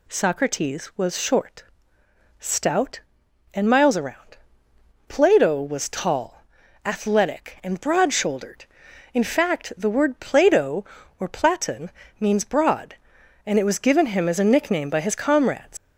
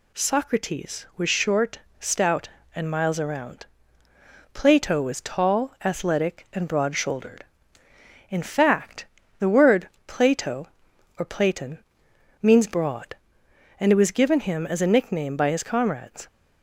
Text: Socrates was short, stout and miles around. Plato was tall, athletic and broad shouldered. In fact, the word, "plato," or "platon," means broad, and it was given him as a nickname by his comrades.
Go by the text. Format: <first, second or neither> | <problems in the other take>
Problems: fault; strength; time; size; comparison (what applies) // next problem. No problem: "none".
second | leaves "comrades" unfinished; at 15.7 s; 115 ms